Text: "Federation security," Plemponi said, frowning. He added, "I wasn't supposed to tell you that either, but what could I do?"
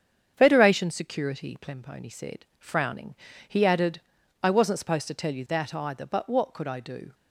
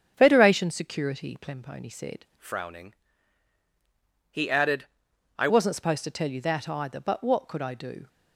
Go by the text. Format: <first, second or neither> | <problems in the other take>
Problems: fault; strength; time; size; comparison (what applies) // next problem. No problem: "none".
first | starts louder than the rest; strong; until 1.1 s; 8 dB; strong in the first // changes voice from "frowning" to "I"; from 2.3 to 5.4 s; 3.1 s long